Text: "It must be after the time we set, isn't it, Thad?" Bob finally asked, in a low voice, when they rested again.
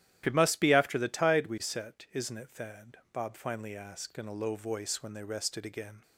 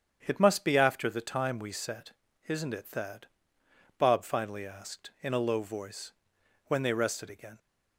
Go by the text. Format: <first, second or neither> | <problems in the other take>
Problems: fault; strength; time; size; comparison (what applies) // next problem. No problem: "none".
second | starts louder than the rest; strong; until 1.2 s; 12 dB; strong in the second // says "tide" for "time"; at 1.0 s